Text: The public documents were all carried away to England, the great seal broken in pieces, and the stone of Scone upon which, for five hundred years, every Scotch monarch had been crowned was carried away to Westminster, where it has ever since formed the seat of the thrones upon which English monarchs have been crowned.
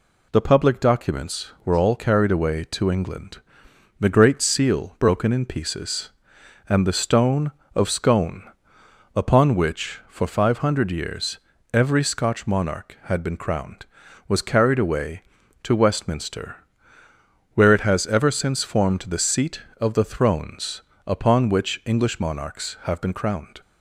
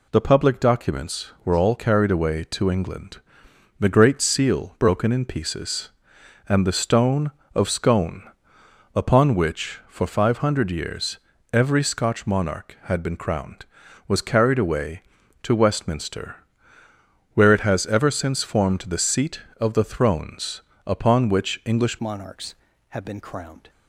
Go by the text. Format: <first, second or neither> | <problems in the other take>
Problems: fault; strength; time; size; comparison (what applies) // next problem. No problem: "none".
first | pauses between "Scone" and "upon"; noticeable; at 8.2 s; 0.72 s long; noticeable in the first // pauses between "thrones" and "upon"; slight; at 20.6 s; 0.24 s long; slight in the first // changes voice at "monarchs"; from 21.9 s on; 1.7 s long